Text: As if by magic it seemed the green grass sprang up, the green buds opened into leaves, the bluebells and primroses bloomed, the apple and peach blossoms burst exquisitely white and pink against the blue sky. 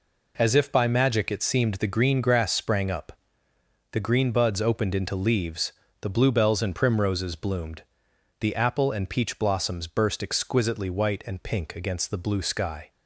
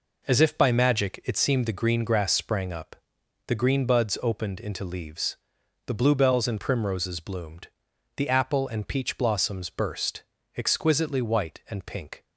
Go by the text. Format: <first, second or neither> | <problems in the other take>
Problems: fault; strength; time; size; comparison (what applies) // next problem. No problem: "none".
first | pauses between "burst" and "exquisitely"; slight; at 10.2 s; 0.34 s long // stops before "against the blue sky"; at 12.2 s